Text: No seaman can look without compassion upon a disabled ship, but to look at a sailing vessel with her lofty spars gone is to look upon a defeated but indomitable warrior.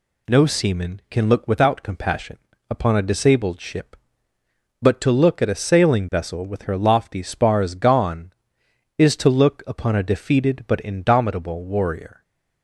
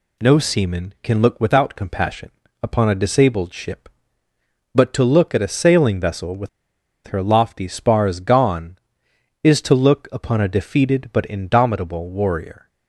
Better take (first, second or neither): first